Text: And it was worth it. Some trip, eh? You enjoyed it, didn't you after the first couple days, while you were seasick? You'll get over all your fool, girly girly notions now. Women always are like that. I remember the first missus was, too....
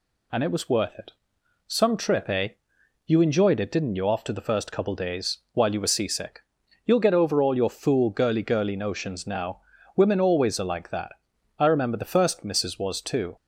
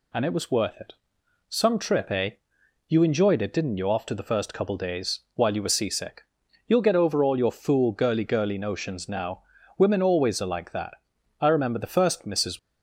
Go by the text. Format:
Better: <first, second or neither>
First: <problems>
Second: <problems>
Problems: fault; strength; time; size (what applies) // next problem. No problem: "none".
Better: first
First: none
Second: stops before "was too"; at 12.5 s